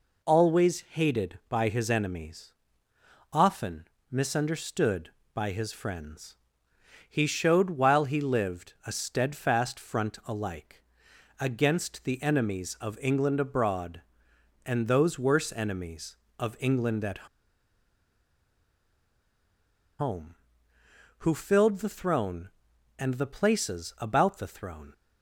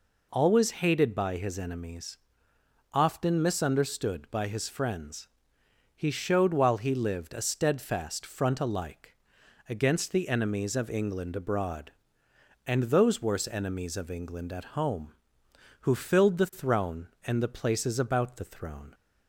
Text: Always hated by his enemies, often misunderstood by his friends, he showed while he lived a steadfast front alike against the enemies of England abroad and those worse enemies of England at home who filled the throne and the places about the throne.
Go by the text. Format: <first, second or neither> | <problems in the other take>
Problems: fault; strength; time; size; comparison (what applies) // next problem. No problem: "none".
second | pauses between "often" and "misunderstood"; slight; at 3.8 s; 0.24 s long // pauses between "alike" and "against"; noticeable; at 10.8 s; 0.56 s long; noticeable in the second // pauses between "at" and "home"; strong; at 17.2 s; 2.7 s long